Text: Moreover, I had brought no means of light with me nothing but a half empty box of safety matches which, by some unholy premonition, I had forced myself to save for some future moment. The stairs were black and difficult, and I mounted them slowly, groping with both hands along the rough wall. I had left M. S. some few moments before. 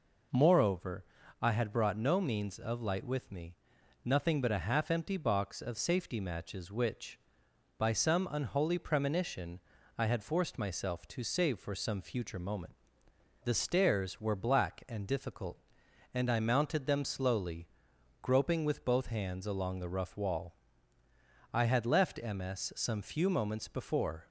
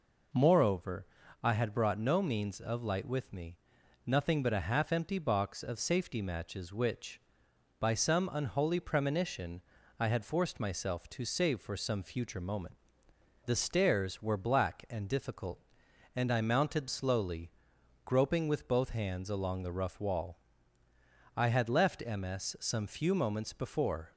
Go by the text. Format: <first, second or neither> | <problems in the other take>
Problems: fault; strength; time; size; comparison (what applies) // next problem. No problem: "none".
first | pauses between "me" and "nothing"; noticeable; at 3.5 s; 0.48 s long; noticeable in the first // skips "them"; at 16.8 s